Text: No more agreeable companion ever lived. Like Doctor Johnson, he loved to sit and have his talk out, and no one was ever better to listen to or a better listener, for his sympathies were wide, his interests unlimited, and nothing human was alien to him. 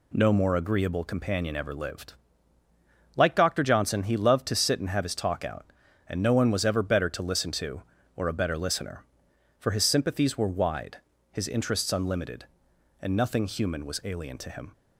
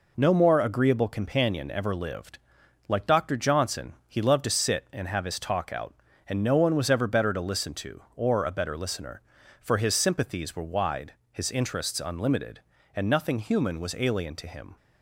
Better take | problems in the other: neither | none

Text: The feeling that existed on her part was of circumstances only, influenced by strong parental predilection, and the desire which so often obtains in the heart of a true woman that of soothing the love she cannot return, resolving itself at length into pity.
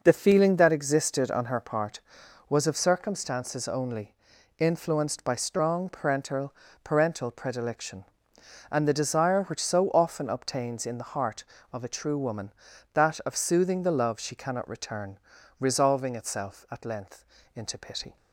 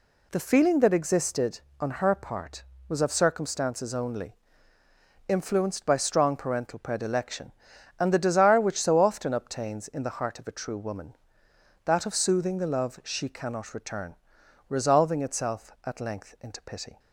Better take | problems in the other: second | says "parental" twice; at 6.8 s // pauses between "length" and "into"; slight; at 17.2 s; 0.28 s long

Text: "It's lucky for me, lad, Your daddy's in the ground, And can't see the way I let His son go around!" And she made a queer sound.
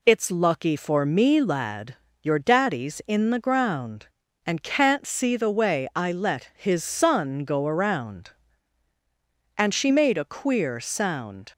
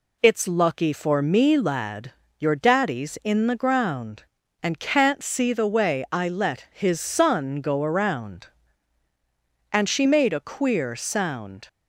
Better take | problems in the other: neither | none

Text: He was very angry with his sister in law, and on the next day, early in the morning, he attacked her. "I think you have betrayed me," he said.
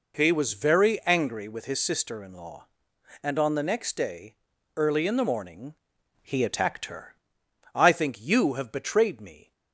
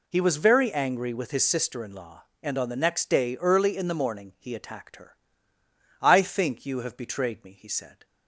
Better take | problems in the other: second | stops before "he said"; at 9.5 s

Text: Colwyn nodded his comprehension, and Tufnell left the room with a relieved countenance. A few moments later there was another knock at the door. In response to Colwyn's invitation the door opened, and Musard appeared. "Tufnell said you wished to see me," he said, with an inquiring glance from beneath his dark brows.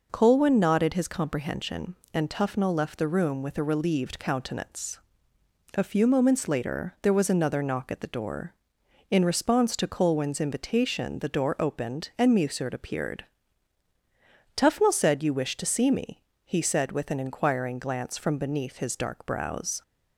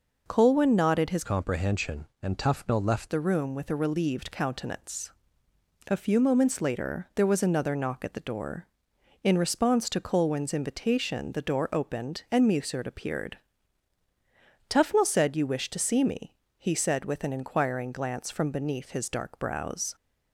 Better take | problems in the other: first | changes voice from "comprehension" to "left"; from 1.2 to 3.1 s; 1.9 s long

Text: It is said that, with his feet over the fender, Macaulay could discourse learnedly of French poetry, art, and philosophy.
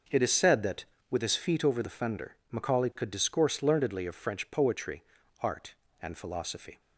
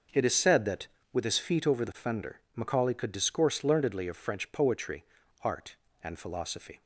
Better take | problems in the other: neither | starts louder than the rest; noticeable; the same in both

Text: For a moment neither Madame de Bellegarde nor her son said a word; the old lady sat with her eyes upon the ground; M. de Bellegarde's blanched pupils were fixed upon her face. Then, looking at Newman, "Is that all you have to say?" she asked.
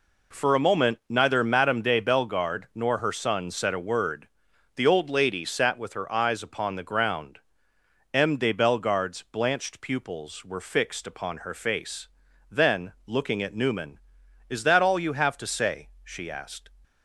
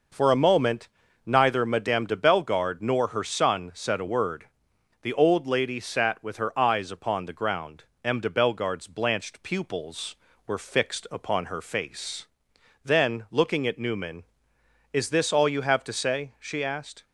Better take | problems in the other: first | pauses between "moment" and "neither"; slight; at 0.8 s; 0.36 s long // says "this" for "that"; at 15.0 s

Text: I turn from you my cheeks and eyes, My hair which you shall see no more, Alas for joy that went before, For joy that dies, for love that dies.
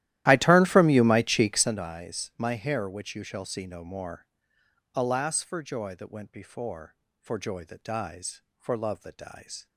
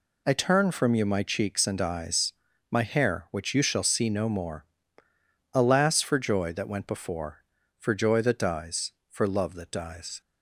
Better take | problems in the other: second | starts louder than the rest; strong; until 1.9 s; 14 dB

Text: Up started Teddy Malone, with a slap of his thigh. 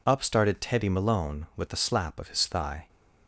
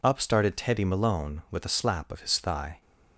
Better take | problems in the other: neither | none

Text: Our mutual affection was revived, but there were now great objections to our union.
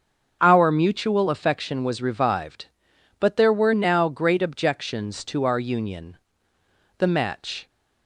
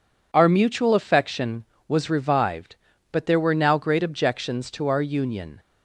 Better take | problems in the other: second | starts louder than the rest; strong; until 1.4 s; 7 dB // goes on to say "The match"; noticeable; from 6.9 s on; 0.70 s long

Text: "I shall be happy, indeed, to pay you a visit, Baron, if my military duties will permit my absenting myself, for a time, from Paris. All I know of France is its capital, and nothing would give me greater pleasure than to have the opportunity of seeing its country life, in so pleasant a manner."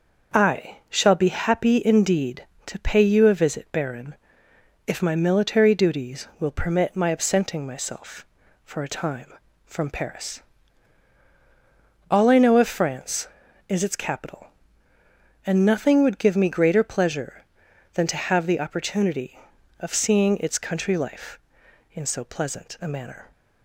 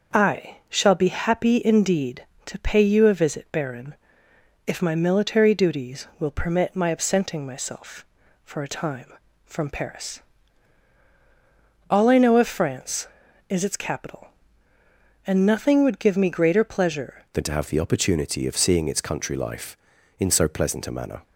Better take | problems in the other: first | changes voice at "than"; from 17.3 s on; 3.9 s long

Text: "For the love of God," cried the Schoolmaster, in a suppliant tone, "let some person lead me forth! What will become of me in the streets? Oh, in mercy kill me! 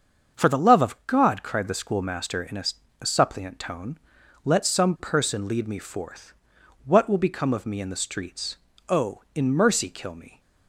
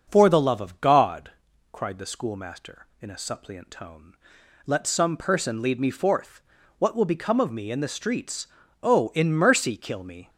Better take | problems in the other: second | starts louder than the rest; until 1.4 s; 7 dB; also in the second // says "a" twice; at 2.9 s

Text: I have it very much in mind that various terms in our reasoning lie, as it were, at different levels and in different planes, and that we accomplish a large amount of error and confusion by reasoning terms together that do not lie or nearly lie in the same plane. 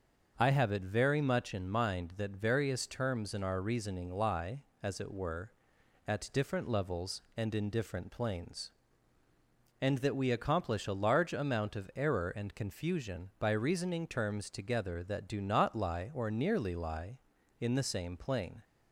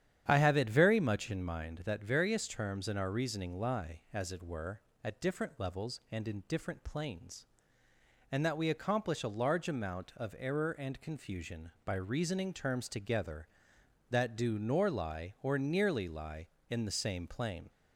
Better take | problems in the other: first | starts louder than the rest; strong; until 1.2 s; 9.5 dB; also in the first // says "nor" for "not"; at 14.5 s

